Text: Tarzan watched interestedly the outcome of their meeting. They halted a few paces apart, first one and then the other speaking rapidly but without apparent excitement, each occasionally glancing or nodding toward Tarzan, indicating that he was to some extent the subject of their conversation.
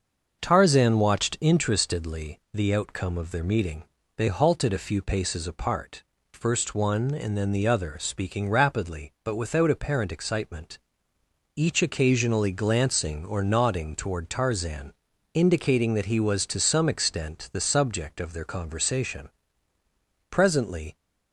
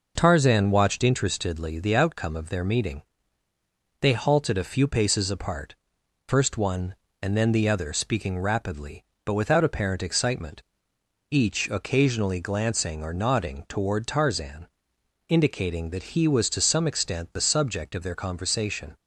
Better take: second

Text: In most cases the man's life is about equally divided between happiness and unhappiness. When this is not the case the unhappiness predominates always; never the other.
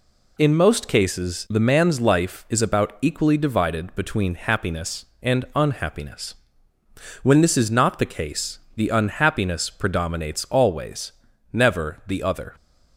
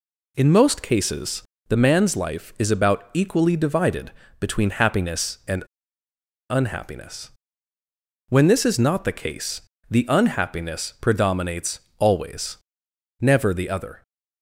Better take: first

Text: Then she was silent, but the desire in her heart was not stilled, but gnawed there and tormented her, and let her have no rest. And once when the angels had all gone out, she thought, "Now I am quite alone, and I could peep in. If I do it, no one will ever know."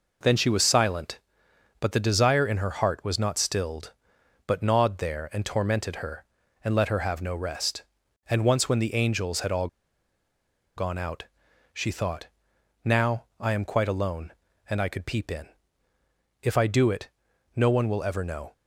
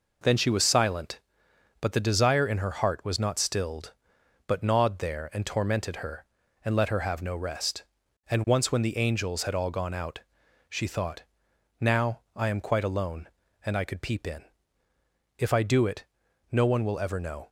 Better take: second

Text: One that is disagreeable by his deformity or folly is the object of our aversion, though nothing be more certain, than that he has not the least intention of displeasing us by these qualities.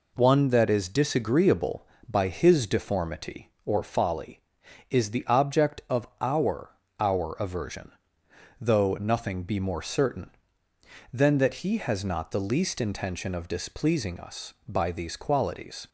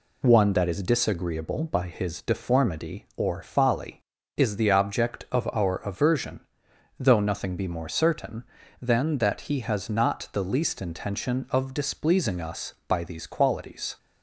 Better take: second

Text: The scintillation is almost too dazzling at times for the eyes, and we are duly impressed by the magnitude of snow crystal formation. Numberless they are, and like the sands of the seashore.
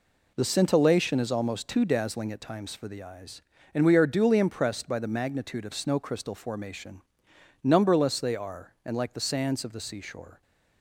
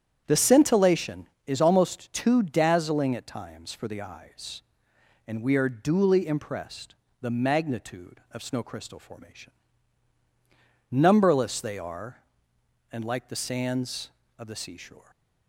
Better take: first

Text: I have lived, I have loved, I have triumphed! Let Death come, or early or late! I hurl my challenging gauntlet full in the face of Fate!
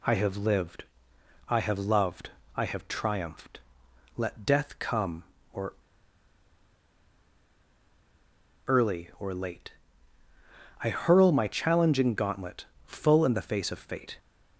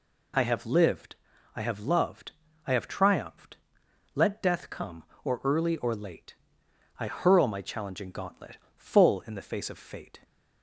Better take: second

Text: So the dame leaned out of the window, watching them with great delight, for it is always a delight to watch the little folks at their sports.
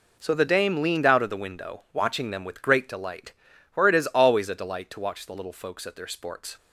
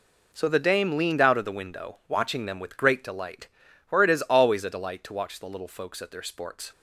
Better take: neither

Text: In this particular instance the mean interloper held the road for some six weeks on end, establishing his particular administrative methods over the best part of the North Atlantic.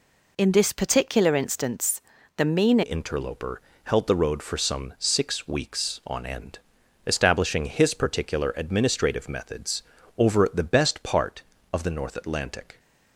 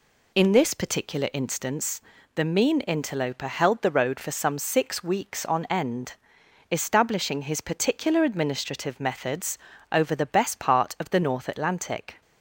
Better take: second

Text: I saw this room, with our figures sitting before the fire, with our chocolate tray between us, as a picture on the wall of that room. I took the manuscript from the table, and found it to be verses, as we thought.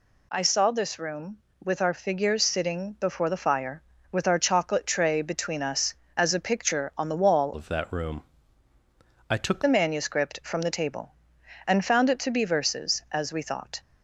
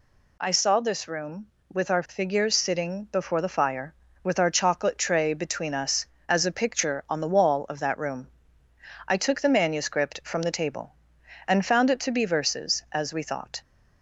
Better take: second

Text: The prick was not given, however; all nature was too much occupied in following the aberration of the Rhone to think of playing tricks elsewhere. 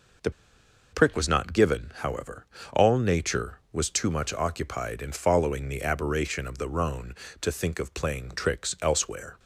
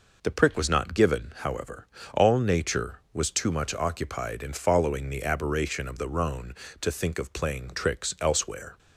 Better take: second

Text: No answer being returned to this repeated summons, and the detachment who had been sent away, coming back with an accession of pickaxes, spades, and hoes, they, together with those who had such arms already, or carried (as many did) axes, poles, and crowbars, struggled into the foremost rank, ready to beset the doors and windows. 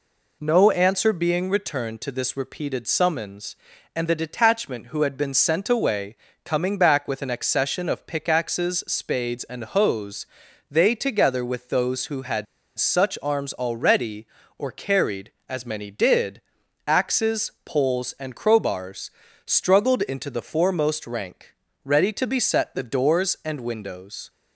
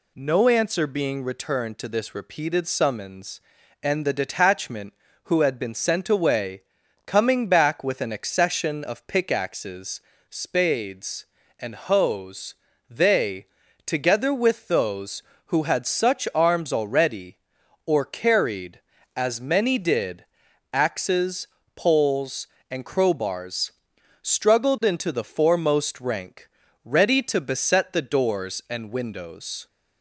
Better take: second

